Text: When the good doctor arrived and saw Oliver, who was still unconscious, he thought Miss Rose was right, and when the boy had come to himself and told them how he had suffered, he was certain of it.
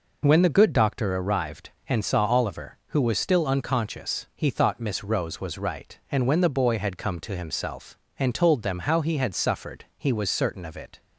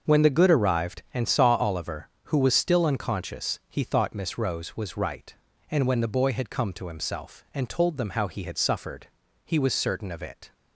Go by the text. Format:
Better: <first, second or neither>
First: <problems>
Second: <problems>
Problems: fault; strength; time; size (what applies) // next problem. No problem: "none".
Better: first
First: none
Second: starts louder than the rest; until 1.1 s; 6.5 dB // skips "doctor"; at 0.5 s